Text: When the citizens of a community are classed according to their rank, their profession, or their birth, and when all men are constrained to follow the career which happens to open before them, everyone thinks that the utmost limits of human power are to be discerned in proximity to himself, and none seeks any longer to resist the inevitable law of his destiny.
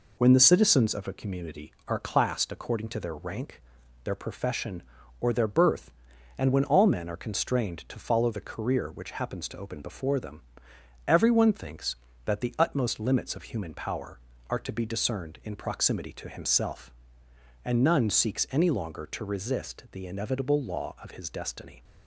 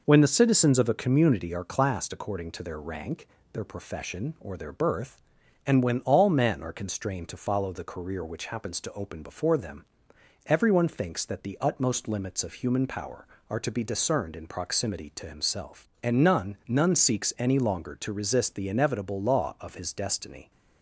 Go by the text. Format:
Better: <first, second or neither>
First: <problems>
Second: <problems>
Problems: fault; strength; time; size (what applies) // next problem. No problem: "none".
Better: first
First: none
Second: says "none" twice; at 16.6 s